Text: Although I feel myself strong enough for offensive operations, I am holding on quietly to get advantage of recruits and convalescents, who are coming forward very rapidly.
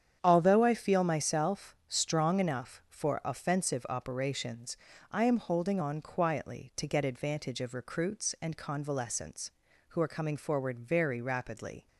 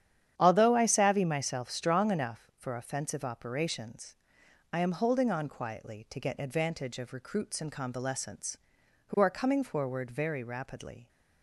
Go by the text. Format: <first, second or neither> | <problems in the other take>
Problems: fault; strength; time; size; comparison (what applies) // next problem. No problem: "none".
first | starts louder than the rest; strong; until 1.3 s; 10 dB; strong in the first // says "savvy" for "feel"; at 0.8 s